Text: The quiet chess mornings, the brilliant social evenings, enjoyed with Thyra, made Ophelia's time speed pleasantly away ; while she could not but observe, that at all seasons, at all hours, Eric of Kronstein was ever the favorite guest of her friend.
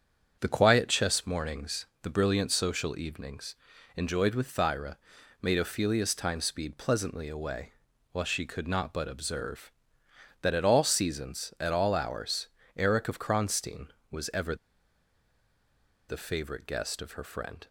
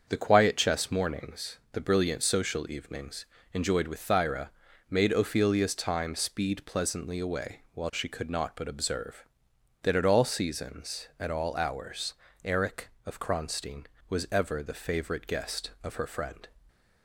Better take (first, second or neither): second